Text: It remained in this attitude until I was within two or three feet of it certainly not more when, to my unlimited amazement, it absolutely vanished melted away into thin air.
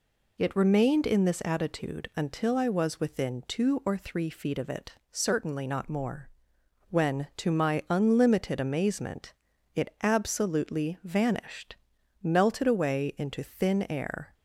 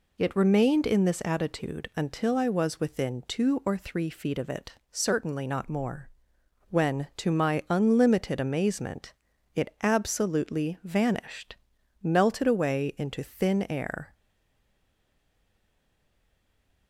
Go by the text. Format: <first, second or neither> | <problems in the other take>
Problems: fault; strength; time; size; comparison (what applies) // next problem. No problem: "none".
first | pauses between "it" and "certainly"; slight; at 4.7 s; 0.18 s long; slight in the first // pauses between "more" and "when"; noticeable; at 6.0 s; 0.60 s long; noticeable in the first // pauses between "vanished" and "melted"; noticeable; at 11.5 s; 0.46 s long; noticeable in the first // stays silent after the last word; strong; from 14.1 s on; 2.7 s long